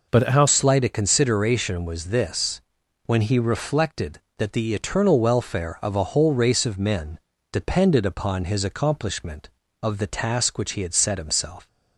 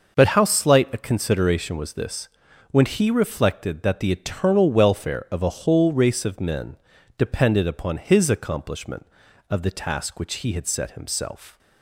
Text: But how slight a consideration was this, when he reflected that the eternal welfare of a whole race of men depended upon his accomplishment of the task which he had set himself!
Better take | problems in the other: second | changes voice at "slight"; from 0.4 s on; 11.2 s long // pauses between "men" and "depended"; slight; at 7.1 s; 0.32 s long; also in the second

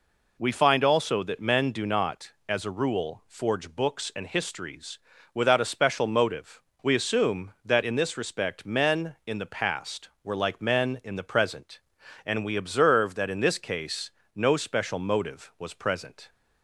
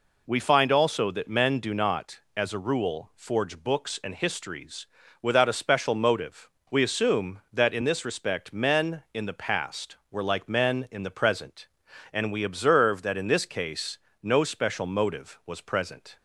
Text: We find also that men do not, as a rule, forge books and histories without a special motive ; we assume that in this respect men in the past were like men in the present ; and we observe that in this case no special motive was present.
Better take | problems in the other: neither | pauses between "histories" and "without"; slight; the same in both // pauses between "case" and "no"; slight; the same in both

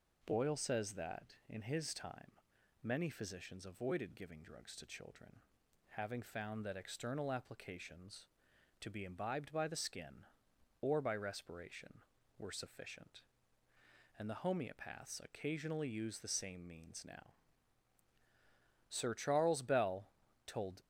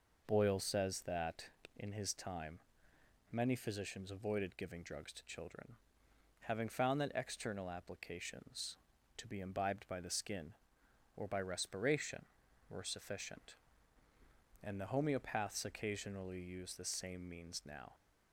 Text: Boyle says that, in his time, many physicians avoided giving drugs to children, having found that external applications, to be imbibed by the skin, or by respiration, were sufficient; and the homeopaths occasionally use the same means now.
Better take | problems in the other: second | goes on to say "Sir Charles Bell told"; strong; from 18.8 s on; 1.9 s long

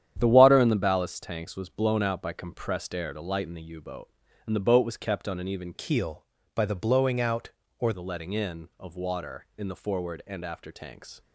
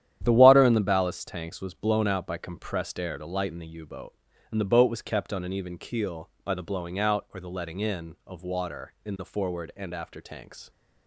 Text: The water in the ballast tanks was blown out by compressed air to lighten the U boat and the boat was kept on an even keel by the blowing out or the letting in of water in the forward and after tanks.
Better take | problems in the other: second | starts louder than the rest; strong; until 1.2 s; 10 dB; strong in the second // changes voice from "keel" to "or"; from 5.7 to 7.9 s; 2.2 s long

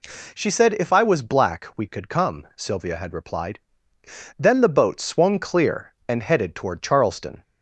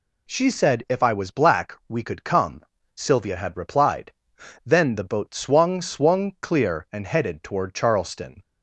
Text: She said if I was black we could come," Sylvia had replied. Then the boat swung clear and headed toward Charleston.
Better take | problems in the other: first | says "swung" twice; at 5.8 s

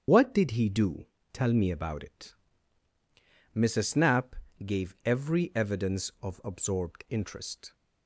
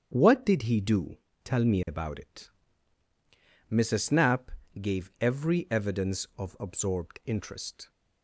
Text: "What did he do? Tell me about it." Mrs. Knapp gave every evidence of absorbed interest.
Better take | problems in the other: second | loses the start of "What"; at 0.0 s; 85 ms // starts louder than the rest; strong; until 1.3 s; 7.5 dB; strong in the second // pauses between "Knapp" and "gave"; slight; at 4.3 s; 0.30 s long; slight in the second

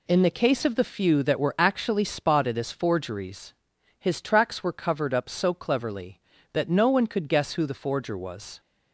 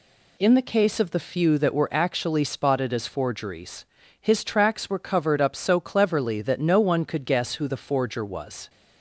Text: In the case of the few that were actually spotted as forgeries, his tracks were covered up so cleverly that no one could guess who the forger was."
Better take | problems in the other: neither | none

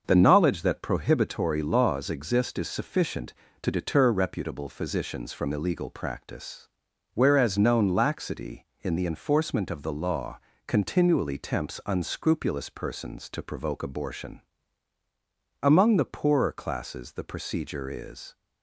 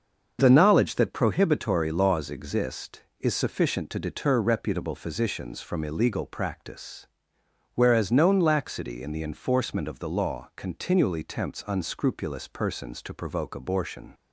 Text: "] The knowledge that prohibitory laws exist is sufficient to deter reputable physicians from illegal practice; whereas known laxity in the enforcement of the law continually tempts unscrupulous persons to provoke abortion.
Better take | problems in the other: second | starts louder than the rest; until 1.0 s; 6 dB; also in the second // pauses between "law" and "continually"; slight; at 10.3 s; 0.30 s long // goes on to say "Among the poorer classes the procedure is"; strong; from 15.5 s on; 2.7 s long

